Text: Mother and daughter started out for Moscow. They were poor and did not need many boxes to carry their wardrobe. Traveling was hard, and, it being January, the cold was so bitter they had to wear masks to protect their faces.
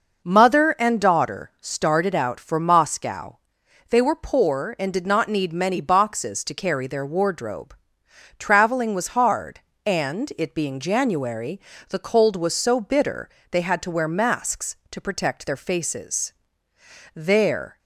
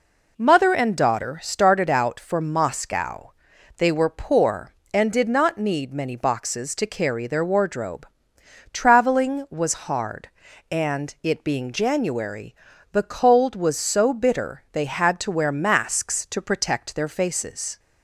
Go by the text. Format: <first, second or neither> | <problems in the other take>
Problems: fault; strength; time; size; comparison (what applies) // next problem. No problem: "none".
second | pauses between "bitter" and "they"; slight; at 13.2 s; 0.22 s long // goes on to say "There"; noticeable; from 17.1 s on; 0.64 s long